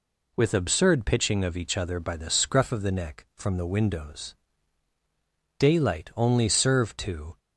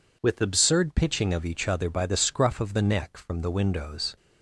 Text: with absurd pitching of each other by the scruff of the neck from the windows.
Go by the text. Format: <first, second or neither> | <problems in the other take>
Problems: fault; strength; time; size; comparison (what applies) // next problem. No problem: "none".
second | goes on to say "Daylight only served to"; strong; from 5.5 s on; 1.8 s long